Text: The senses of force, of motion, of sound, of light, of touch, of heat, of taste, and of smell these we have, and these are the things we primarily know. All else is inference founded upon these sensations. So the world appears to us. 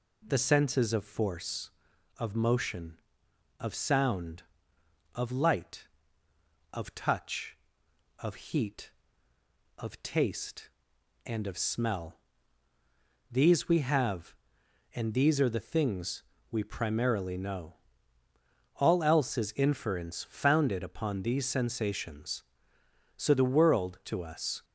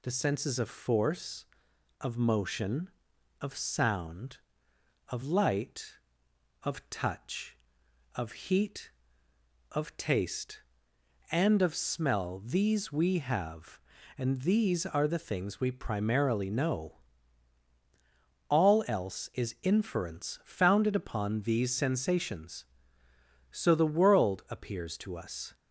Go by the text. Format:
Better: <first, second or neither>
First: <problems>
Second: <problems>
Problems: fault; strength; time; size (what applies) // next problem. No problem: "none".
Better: second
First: pauses between "smell" and "these"; at 12.1 s; 1.1 s long // pauses between "things" and "we"; slight; at 16.2 s; 0.30 s long // skips "appears"; at 24.0 s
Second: none